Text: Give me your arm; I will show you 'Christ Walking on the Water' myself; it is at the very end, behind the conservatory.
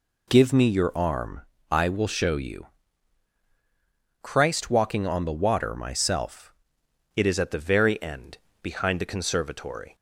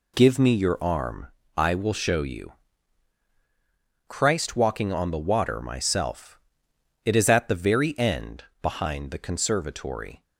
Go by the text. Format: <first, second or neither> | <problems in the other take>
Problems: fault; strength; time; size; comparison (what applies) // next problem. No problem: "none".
second | pauses between "you" and "Christ"; strong; at 2.6 s; 1.5 s long; strong in the second // changes voice at "it"; from 7.1 s on; 2.8 s long